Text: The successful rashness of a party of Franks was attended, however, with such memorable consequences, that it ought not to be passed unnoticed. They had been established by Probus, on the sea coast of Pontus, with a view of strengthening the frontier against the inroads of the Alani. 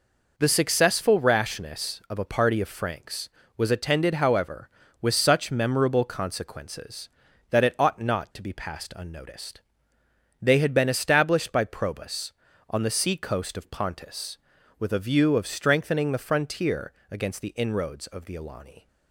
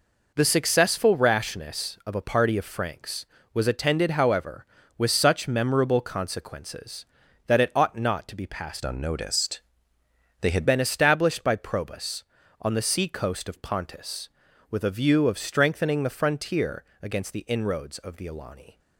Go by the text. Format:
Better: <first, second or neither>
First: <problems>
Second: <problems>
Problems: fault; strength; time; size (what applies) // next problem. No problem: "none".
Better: first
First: pauses between "frontier" and "against"; slight; at 16.9 s; 0.18 s long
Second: changes voice from "unnoticed" to "had"; from 8.8 to 10.6 s; 1.8 s long // pauses between "frontier" and "against"; slight; at 16.8 s; 0.18 s long